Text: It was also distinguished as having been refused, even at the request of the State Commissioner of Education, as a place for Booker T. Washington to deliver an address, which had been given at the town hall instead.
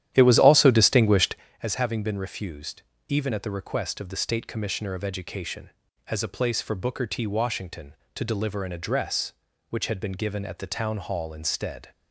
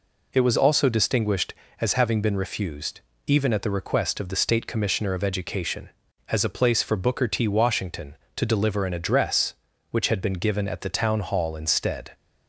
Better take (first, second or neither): second